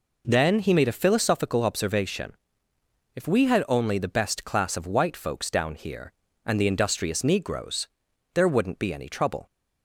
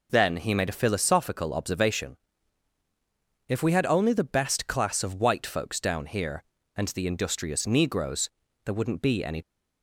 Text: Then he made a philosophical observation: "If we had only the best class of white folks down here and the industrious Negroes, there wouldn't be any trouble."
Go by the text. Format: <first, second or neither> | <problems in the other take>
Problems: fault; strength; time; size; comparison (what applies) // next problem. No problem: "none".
first | stops before "trouble"; at 9.4 s